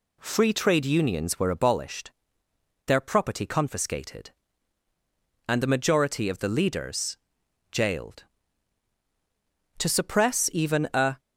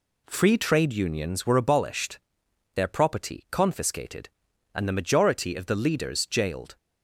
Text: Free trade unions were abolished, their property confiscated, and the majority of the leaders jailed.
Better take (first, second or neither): second